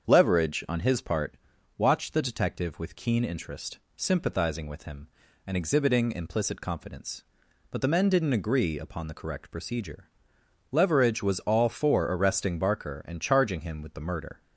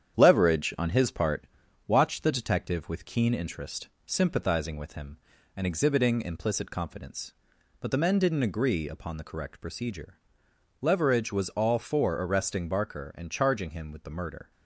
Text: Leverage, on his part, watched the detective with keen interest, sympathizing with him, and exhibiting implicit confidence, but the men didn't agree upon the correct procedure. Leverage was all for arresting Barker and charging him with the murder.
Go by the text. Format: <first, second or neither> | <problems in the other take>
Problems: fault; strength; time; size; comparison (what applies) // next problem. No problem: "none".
first | gets quieter; noticeable; throughout; 4.5 dB // starts louder than the rest; strong; until 1.2 s; 9 dB; strong in the first